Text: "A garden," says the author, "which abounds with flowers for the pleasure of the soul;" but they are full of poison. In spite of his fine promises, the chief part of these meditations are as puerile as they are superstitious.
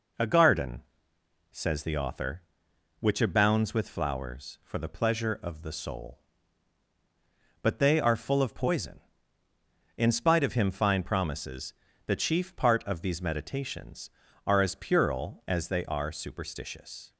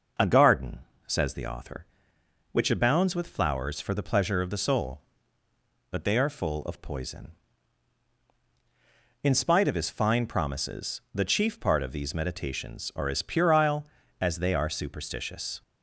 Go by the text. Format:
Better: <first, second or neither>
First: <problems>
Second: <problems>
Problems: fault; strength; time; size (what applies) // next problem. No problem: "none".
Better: second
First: says "him" for "his"; at 10.5 s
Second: none